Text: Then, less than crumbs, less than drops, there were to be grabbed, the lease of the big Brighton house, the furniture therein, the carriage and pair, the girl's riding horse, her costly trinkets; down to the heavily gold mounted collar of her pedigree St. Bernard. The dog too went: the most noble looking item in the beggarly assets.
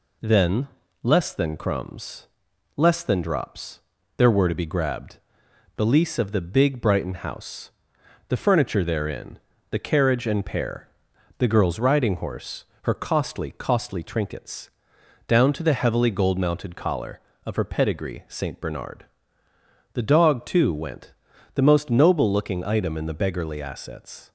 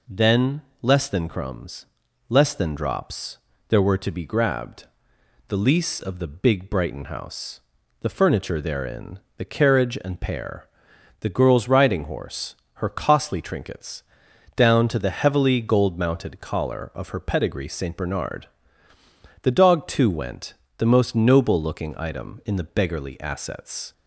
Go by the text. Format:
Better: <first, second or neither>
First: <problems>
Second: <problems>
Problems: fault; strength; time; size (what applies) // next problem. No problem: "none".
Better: second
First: says "costly" twice; at 13.5 s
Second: none